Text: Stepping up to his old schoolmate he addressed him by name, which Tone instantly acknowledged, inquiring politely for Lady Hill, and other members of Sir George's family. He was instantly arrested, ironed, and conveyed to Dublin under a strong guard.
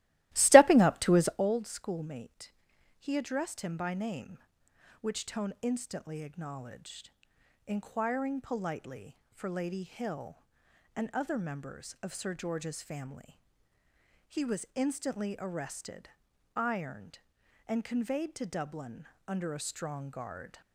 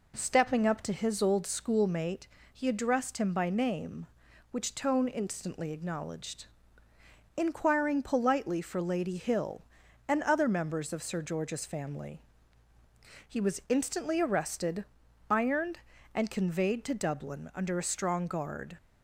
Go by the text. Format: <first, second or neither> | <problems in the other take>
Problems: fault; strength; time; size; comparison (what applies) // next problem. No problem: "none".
second | starts louder than the rest; strong; until 1.5 s; 17 dB // pauses between "schoolmate" and "he"; noticeable; at 2.5 s; 0.46 s long; slight in the second // pauses between "Dublin" and "under"; slight; at 19.0 s; 0.20 s long